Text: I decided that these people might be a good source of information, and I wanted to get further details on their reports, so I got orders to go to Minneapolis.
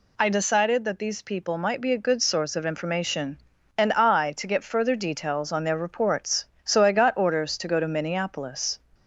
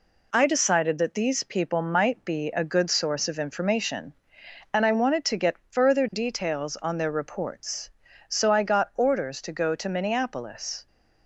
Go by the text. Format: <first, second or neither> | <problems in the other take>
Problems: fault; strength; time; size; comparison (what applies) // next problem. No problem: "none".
second | skips "wanted"; at 4.3 s